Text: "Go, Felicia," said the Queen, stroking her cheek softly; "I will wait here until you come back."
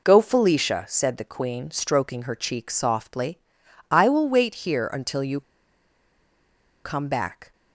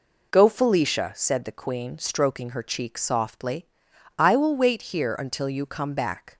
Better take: second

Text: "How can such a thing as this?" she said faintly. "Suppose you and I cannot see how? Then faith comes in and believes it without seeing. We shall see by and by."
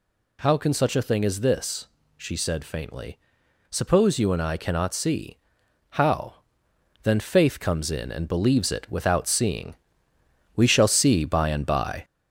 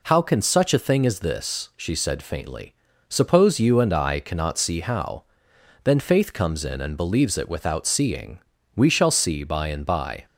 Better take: second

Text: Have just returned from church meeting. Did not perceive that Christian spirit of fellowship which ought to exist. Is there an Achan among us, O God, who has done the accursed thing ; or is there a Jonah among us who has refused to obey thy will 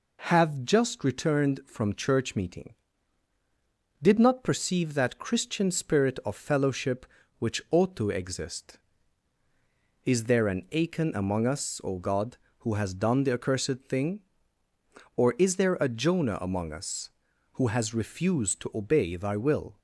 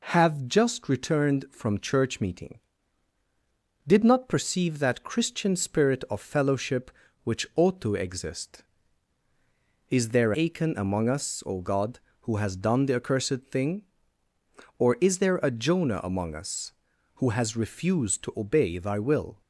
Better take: first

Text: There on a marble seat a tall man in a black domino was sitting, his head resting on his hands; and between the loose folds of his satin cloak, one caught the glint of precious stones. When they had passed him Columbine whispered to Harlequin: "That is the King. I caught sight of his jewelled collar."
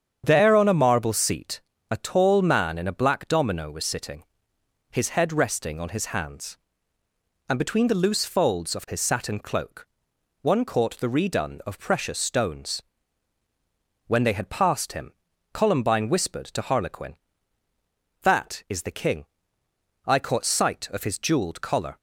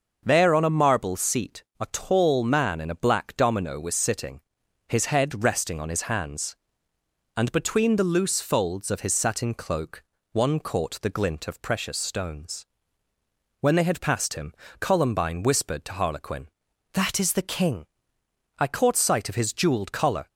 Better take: second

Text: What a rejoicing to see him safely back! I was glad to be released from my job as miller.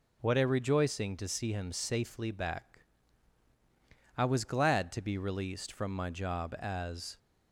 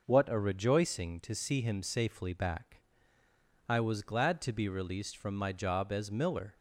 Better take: second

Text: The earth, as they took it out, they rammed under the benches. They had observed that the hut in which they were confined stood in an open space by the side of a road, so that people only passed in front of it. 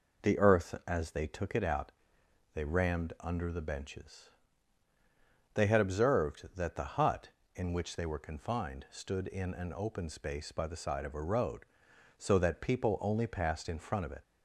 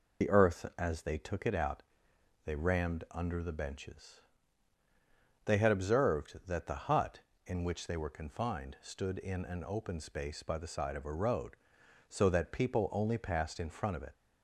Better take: first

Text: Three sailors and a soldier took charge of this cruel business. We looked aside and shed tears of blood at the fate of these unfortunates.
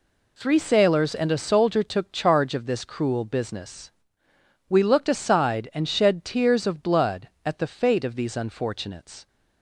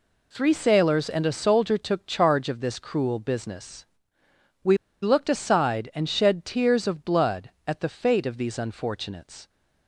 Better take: first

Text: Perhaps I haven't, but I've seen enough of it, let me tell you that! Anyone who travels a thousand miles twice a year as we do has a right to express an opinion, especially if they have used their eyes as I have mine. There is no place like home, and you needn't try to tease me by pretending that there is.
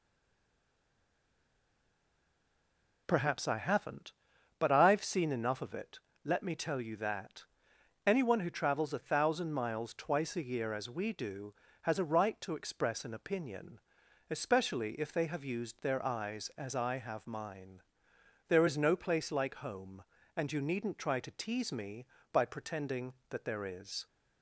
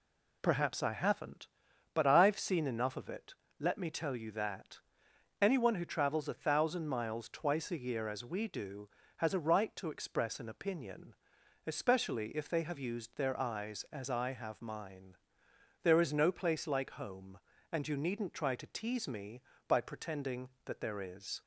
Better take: second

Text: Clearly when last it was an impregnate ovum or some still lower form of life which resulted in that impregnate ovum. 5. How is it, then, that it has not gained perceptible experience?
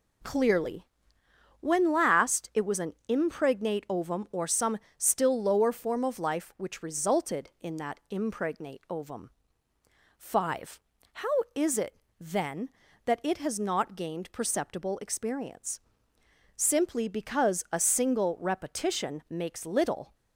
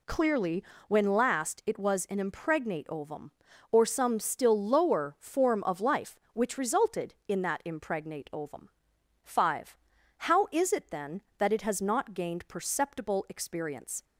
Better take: second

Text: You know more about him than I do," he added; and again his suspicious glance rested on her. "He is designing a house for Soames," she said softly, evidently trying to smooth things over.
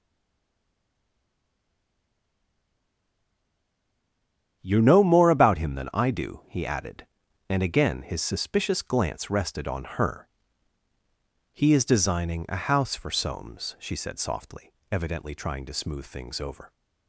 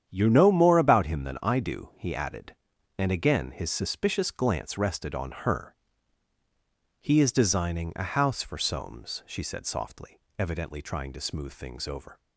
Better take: second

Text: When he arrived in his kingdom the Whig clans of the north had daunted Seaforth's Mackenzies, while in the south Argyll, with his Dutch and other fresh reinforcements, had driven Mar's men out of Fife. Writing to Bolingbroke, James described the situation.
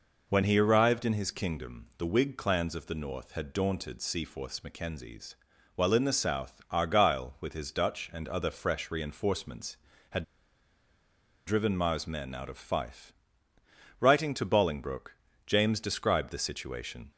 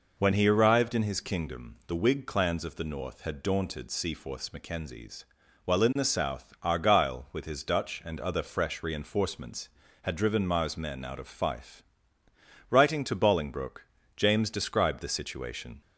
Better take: second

